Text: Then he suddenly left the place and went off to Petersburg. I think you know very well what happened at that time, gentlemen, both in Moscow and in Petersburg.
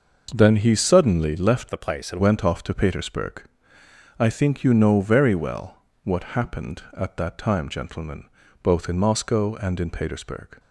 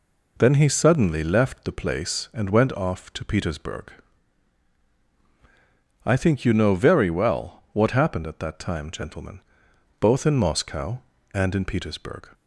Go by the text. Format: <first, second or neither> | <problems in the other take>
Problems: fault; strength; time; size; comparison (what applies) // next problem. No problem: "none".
second | starts louder than the rest; noticeable; until 1.3 s; 6 dB // changes voice from "the" to "and"; from 1.7 to 2.2 s; 0.5 s long // pauses between "well" and "what"; slight; at 5.7 s; 0.26 s long